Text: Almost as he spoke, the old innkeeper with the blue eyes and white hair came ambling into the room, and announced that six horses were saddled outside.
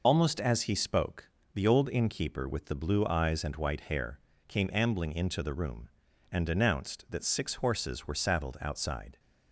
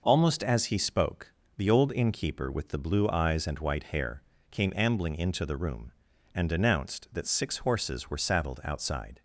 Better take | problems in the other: second | loses the start of "Almost"; at 0.0 s; 50 ms // pauses between "hair" and "came"; slight; at 4.1 s; 0.28 s long; slight in the second

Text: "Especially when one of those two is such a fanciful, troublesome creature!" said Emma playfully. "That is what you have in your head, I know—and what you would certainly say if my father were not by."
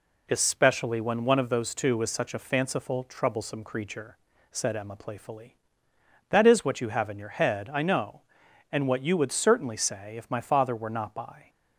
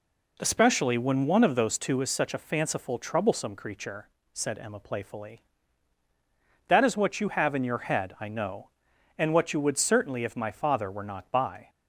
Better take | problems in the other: first | skips "say"; at 10.2 s

